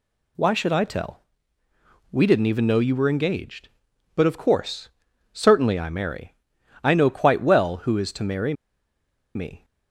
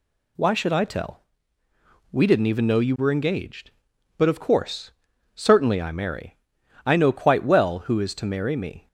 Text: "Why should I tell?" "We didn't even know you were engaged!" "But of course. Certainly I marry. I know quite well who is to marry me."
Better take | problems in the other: second | pauses between "marry" and "me"; noticeable; at 8.5 s; 0.82 s long

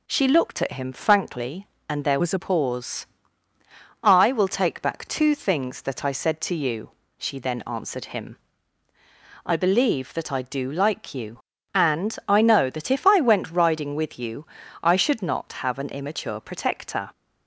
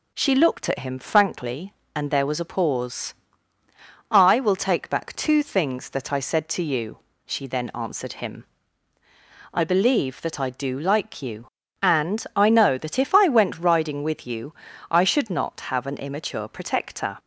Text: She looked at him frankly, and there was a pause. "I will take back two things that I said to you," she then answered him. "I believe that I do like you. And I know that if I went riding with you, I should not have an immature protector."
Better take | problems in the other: second | changes voice from "was" to "a"; from 2.2 to 2.3 s; 0.1 s long

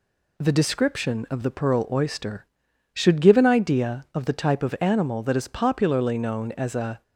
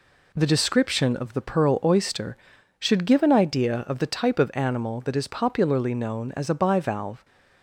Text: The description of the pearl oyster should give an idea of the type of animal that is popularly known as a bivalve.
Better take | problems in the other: second | stops before "bivalve"; at 7.0 s

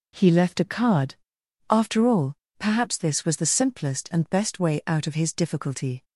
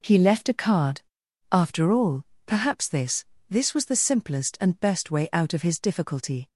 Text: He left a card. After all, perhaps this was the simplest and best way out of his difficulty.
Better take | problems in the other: first | says "this" twice; at 3.4 s

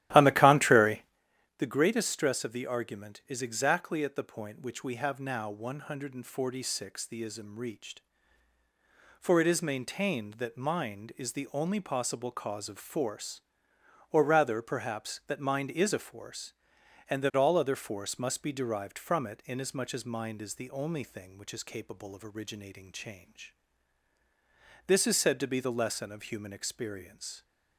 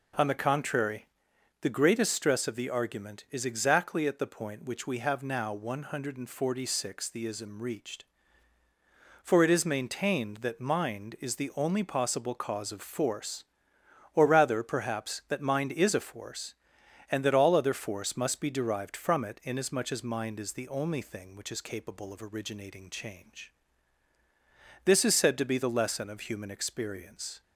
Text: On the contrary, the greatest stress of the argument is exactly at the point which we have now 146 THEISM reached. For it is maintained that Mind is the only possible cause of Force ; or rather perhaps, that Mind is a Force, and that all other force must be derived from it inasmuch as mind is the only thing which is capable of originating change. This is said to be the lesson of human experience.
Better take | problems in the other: second | starts louder than the rest; strong; until 1.3 s; 14 dB

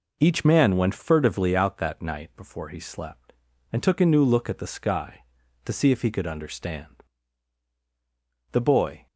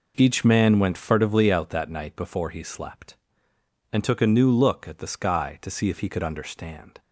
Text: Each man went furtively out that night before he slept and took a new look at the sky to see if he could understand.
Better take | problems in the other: second | goes on to say "The Boy"; from 8.5 s on; 0.54 s long

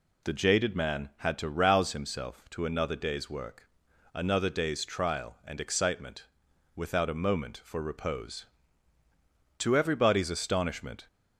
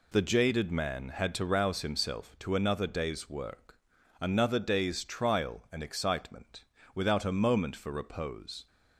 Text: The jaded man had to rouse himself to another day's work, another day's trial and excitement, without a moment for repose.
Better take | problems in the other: second | goes on to say "To everybody's astonishment"; from 9.5 s on; 1.4 s long

